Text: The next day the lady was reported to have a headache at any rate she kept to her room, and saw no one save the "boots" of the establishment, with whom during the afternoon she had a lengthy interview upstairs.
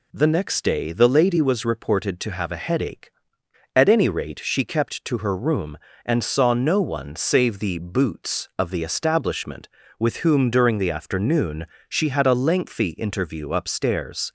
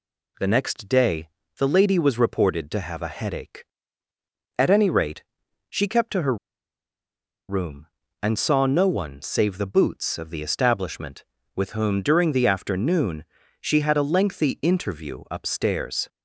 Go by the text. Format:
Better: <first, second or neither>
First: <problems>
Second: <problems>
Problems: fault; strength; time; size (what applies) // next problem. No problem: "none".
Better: first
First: pauses between "afternoon" and "she"; slight; at 11.6 s; 0.20 s long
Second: pauses between "day" and "the"; slight; at 1.2 s; 0.30 s long // pauses between "rate" and "she"; noticeable; at 5.2 s; 0.46 s long // pauses between "her" and "room"; at 6.3 s; 1.1 s long // pauses between "afternoon" and "she"; slight; at 13.2 s; 0.36 s long